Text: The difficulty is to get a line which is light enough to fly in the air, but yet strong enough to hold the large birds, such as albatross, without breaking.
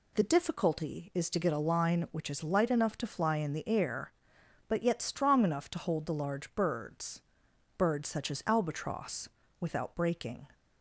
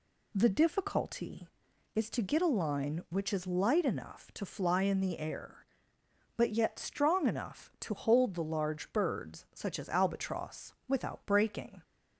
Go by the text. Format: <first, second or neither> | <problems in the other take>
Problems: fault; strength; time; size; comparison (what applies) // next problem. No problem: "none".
second | says "birds" twice; at 7.7 s